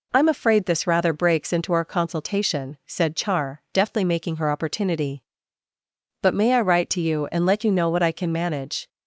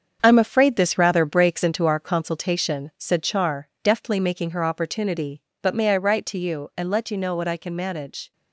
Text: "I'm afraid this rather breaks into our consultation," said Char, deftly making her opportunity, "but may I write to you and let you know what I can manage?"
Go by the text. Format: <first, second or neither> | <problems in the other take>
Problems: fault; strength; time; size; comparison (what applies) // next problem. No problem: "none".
first | gets quieter; strong; throughout; 7.5 dB